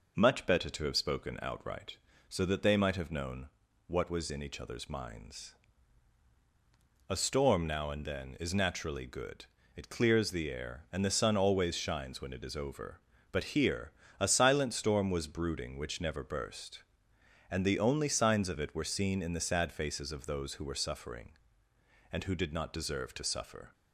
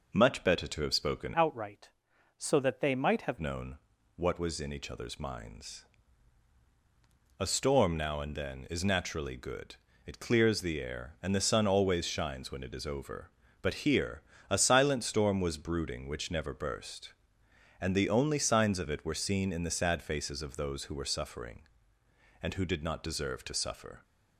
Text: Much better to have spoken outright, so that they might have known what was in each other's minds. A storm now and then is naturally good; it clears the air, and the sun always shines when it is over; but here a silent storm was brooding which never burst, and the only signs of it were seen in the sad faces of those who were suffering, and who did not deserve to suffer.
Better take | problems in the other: first | changes voice from "outright" to "have"; from 1.3 to 3.3 s; 2.0 s long // pauses between "known" and "what"; at 3.7 s; 0.40 s long; also in the first // pauses between "here" and "a"; slight; at 14.2 s; 0.30 s long; slight in the first

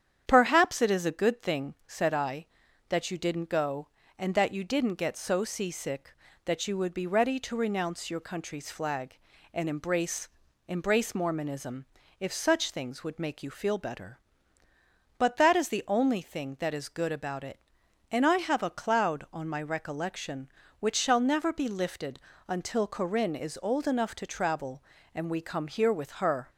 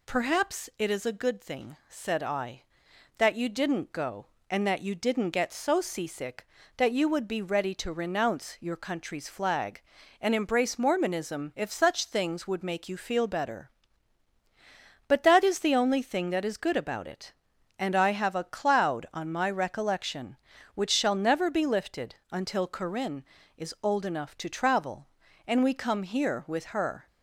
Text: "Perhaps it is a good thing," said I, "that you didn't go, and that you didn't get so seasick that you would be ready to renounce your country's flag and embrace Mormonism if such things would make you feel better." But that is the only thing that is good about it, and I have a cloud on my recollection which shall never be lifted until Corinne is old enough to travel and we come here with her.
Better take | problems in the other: second | starts louder than the rest; strong; until 1.2 s; 9 dB // says "embrace" twice; at 10.6 s // pauses between "Mormonism" and "if"; slight; at 11.8 s; 0.32 s long // pauses between "lifted" and "until"; slight; at 22.1 s; 0.30 s long; slight in the second

